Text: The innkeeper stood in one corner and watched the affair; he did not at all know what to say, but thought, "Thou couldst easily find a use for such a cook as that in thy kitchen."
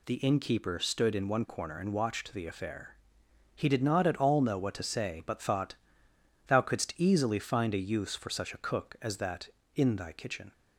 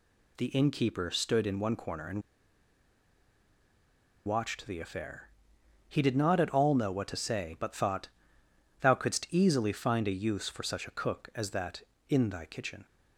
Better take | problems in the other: first | pauses between "and" and "watched"; strong; at 2.2 s; 2.0 s long

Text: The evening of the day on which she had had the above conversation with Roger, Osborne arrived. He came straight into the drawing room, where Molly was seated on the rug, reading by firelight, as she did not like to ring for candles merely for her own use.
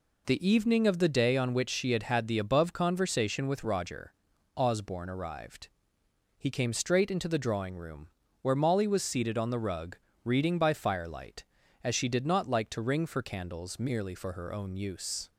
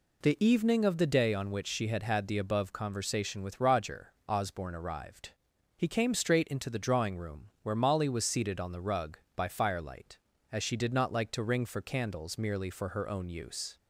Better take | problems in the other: first | skips "reading"; at 9.2 s

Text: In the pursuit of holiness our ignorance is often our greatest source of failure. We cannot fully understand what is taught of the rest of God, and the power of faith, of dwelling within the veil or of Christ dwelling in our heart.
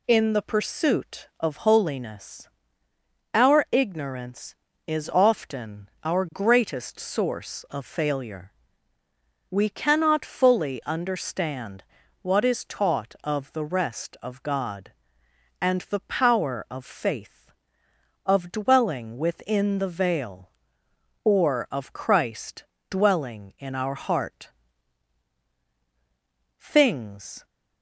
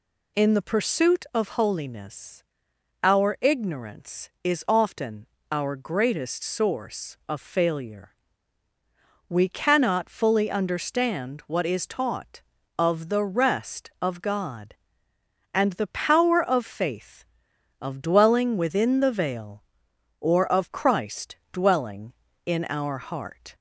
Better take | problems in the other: second | pauses between "holiness" and "our"; noticeable; at 2.4 s; 0.82 s long; noticeable in the second // pauses between "often" and "our"; slight; at 5.8 s; 0.16 s long; slight in the second // pauses between "understand" and "what"; at 11.8 s; 0.38 s long // pauses between "Christ" and "dwelling"; slight; at 22.6 s; 0.26 s long; slight in the second // goes on to say "Things"; noticeable; from 26.6 s on; 0.84 s long

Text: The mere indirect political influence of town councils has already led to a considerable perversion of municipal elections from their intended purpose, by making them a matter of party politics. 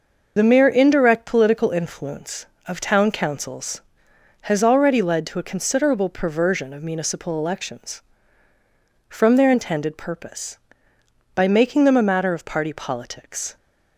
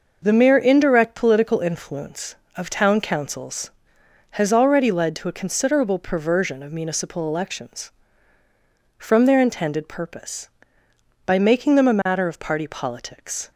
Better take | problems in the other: second | loses the start of "The"; at 0.3 s; 35 ms

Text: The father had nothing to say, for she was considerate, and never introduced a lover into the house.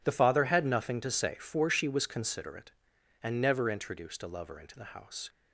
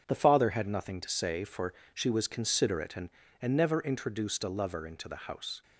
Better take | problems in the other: first | starts louder than the rest; strong; until 1.0 s; 7.5 dB // pauses between "for" and "she"; slight; at 1.7 s; 0.22 s long // says "and" twice; at 3.3 s

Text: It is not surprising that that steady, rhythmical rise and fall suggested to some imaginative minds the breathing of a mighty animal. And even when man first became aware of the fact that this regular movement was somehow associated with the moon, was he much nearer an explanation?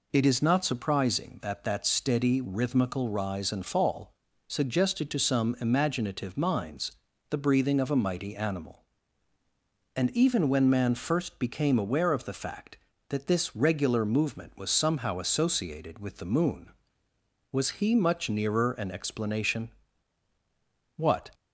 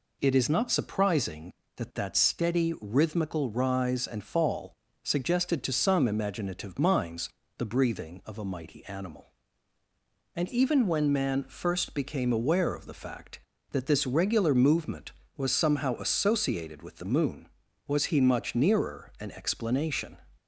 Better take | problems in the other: second | pauses between "fall" and "suggested"; slight; at 4.1 s; 0.36 s long; slight in the second // pauses between "minds" and "the"; at 6.9 s; 0.38 s long; slight in the second // goes on to say "What"; slight; from 20.9 s on; 0.34 s long

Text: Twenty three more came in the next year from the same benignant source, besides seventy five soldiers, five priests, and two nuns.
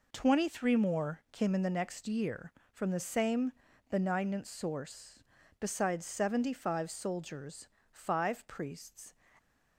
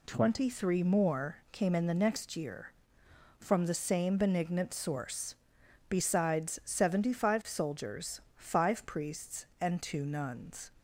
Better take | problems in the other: second | pauses between "same" and "benignant"; at 3.5 s; 0.38 s long // stops before "and two nuns"; at 9.3 s

